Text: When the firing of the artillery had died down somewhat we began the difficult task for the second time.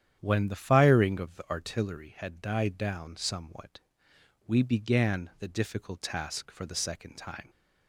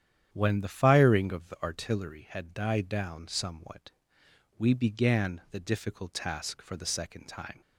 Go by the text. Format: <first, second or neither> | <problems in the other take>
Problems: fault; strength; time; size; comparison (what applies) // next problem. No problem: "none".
neither | starts louder than the rest; strong; the same in both // pauses between "somewhat" and "we"; noticeable; the same in both